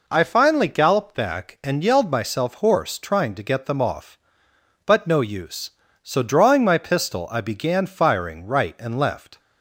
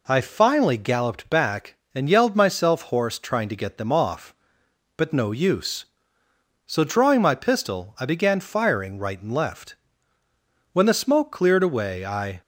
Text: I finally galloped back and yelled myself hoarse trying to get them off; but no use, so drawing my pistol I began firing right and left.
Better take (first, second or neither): first